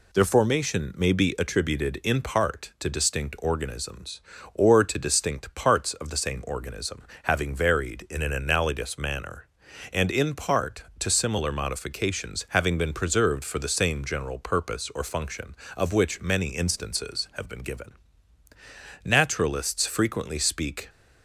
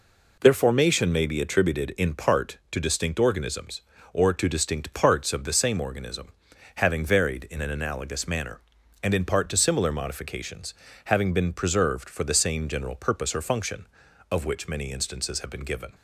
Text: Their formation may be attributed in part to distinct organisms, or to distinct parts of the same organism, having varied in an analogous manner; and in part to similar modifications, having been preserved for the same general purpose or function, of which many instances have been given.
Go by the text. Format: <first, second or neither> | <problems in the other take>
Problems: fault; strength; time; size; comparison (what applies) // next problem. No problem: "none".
second | goes on to say "Naturalists frequently speak"; strong; from 19.0 s on; 1.8 s long